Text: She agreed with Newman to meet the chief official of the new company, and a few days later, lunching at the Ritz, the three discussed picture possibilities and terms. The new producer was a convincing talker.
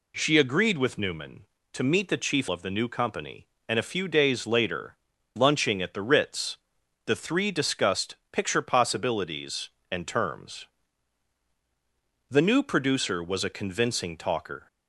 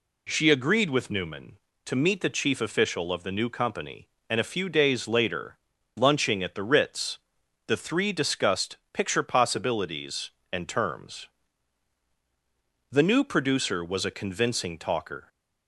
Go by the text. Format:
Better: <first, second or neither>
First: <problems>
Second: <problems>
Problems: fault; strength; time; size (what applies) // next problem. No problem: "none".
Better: second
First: skips "official"; at 2.4 s // pauses between "discussed" and "picture"; slight; at 8.1 s; 0.16 s long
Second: pauses between "discussed" and "picture"; slight; at 8.7 s; 0.16 s long